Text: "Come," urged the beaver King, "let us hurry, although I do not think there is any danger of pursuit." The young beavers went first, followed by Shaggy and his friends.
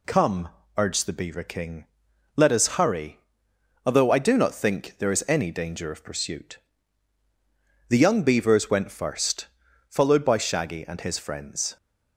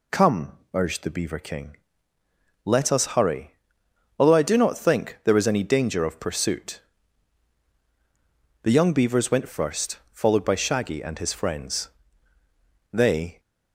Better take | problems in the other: first | goes on to say "They"; slight; from 12.9 s on; 0.48 s long

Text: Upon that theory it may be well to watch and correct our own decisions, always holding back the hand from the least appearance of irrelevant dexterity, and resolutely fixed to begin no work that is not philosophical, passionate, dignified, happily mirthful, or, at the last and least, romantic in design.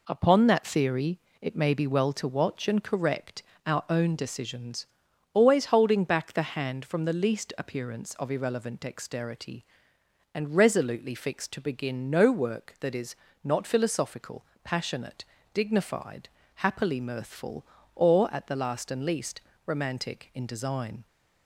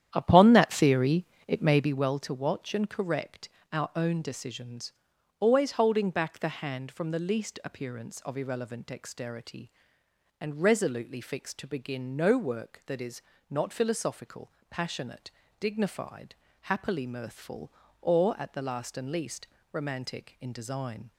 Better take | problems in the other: first | starts louder than the rest; strong; until 2.1 s; 10.5 dB // pauses between "theory" and "it"; slight; at 1.2 s; 0.24 s long; slight in the first // pauses between "correct" and "our"; slight; at 3.4 s; 0.24 s long; slight in the first // pauses between "is" and "not"; slight; at 13.2 s; 0.26 s long; slight in the first

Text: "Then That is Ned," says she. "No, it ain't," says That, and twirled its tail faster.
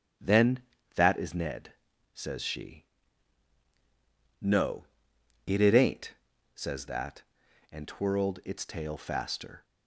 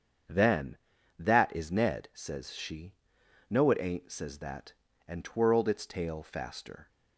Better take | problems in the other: second | starts louder than the rest; strong; until 1.5 s; 9.5 dB; strong in the second // says "it" twice; at 5.6 s

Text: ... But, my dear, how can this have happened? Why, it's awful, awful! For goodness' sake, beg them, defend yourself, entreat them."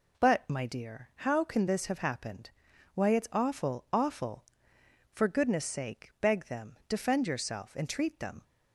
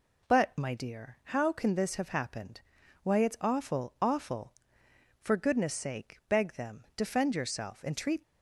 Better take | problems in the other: first | stops before "them"; at 8.2 s

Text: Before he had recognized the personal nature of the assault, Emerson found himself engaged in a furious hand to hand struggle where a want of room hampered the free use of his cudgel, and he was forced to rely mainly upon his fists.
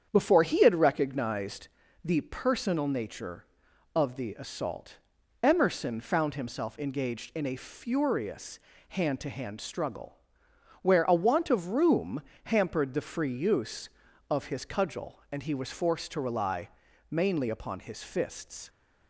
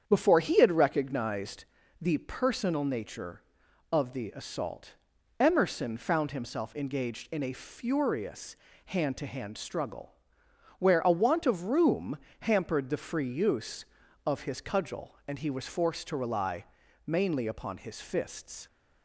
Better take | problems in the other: neither | starts louder than the rest; strong; the same in both // pauses between "recognized" and "the"; slight; the same in both // pauses between "furious" and "hand"; slight; the same in both // pauses between "struggle" and "where"; noticeable; the same in both // pauses between "room" and "hampered"; slight; the same in both // pauses between "rely" and "mainly"; the same in both

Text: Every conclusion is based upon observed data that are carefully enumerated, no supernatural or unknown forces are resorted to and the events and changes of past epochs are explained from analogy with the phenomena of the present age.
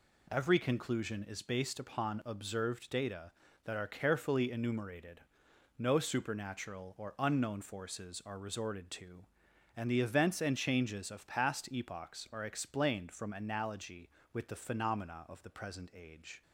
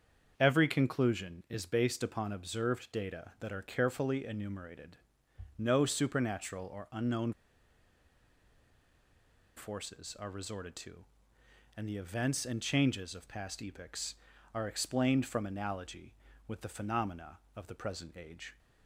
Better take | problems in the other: first | starts louder than the rest; strong; until 1.3 s; 7 dB // pauses between "unknown" and "forces"; strong; at 7.3 s; 2.2 s long

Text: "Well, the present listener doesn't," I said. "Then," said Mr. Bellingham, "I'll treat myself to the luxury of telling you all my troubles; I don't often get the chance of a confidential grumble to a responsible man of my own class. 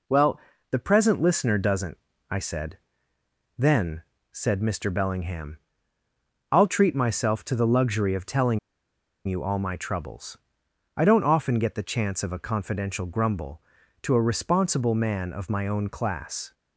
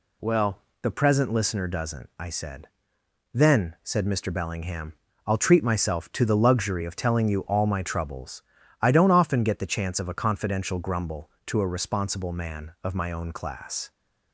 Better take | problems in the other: second | pauses between "telling" and "you"; noticeable; at 8.5 s; 0.68 s long

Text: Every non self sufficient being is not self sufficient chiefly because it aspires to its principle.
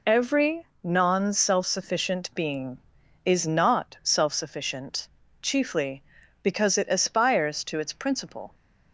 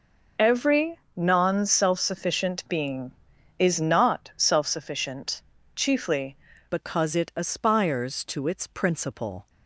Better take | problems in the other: first | pauses between "Every" and "non"; slight; at 0.9 s; 0.18 s long; slight in the first // pauses between "sufficient" and "chiefly"; slight; at 5.3 s; 0.36 s long; slight in the first // changes voice at "because"; from 6.6 s on; 2.8 s long

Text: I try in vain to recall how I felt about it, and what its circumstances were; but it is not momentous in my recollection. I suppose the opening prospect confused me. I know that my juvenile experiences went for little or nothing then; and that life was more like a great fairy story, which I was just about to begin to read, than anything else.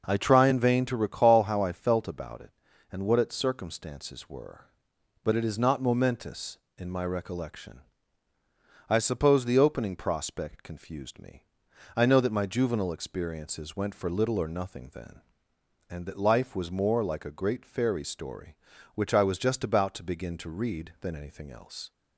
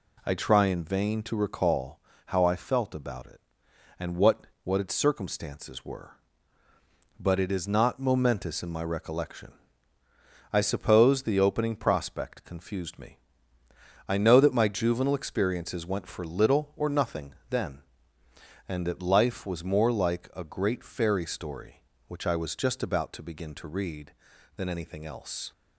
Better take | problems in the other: first | pauses between "recall" and "how"; slight; at 2.0 s; 0.26 s long // says "what" twice; at 4.6 s // pauses between "nothing" and "then"; slight; at 17.3 s; 0.16 s long

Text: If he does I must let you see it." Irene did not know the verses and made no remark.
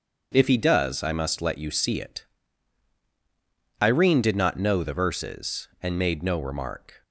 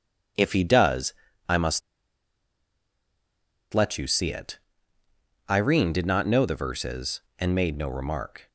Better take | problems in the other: first | pauses between "does" and "I"; slight; at 1.1 s; 0.36 s long // pauses between "must" and "let"; strong; at 1.8 s; 1.9 s long

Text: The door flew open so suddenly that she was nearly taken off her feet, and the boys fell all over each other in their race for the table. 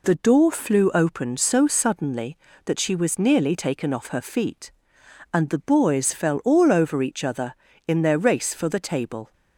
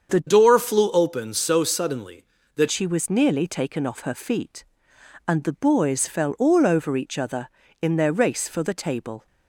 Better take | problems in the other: first | starts louder than the rest; strong; until 1.1 s; 7 dB // changes voice from "door" to "that"; from 0.2 to 2.6 s; 2.4 s long

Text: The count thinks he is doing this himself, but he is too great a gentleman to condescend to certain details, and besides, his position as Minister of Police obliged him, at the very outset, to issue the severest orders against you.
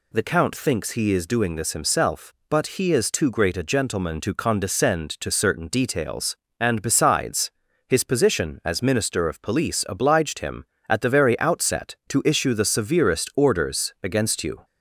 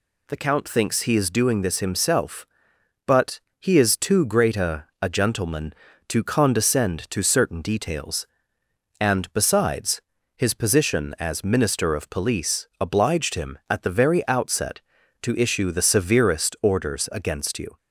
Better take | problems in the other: first | pauses between "but" and "he"; slight; at 3.4 s; 0.18 s long // says "a" twice; at 5.0 s

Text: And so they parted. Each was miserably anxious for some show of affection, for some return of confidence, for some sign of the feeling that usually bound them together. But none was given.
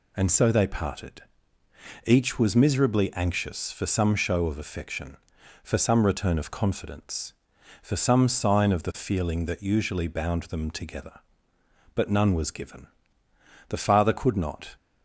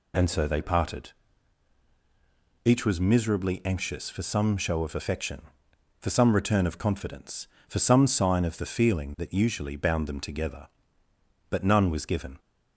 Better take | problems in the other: second | goes on to say "The father could not"; noticeable; from 13.6 s on; 1.0 s long

